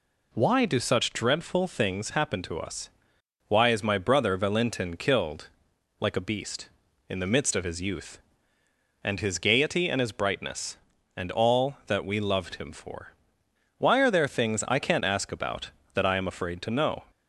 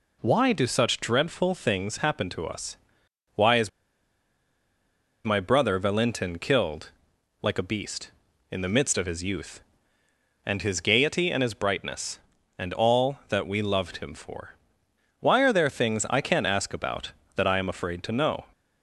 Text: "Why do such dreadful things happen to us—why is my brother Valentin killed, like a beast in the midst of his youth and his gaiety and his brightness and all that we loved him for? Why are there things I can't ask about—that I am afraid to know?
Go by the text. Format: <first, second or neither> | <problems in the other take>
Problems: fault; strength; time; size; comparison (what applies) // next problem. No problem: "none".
first | pauses between "is" and "my"; strong; at 3.6 s; 1.5 s long